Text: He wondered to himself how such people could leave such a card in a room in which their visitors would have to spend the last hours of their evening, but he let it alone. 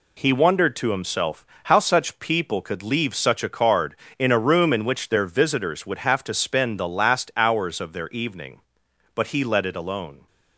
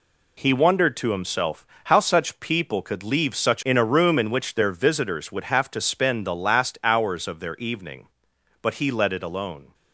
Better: first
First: pauses between "himself" and "how"; slight; at 1.4 s; 0.16 s long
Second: pauses between "himself" and "how"; slight; at 1.6 s; 0.16 s long // skips "a card"; at 3.6 s

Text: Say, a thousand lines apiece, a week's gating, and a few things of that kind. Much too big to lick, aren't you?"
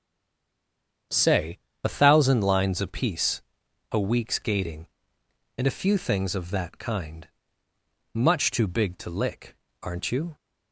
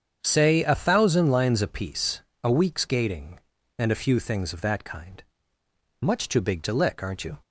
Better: second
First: stays silent before the first word; until 1.1 s; 1.1 s long // starts louder than the rest; strong; until 2.3 s; 8 dB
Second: starts louder than the rest; strong; until 1.2 s; 8 dB

